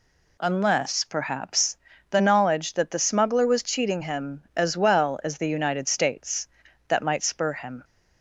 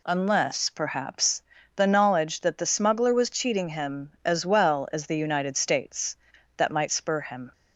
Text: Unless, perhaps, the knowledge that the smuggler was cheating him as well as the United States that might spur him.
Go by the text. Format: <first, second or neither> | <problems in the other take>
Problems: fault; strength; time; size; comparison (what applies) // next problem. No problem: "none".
neither | none